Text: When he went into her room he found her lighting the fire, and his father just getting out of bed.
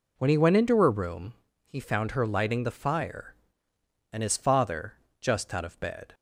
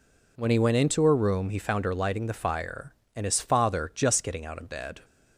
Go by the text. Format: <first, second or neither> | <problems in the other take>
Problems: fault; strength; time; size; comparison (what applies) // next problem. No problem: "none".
second | pauses between "room" and "he"; slight; at 1.3 s; 0.32 s long // pauses between "father" and "just"; slight; at 4.9 s; 0.26 s long // skips "getting"; at 5.5 s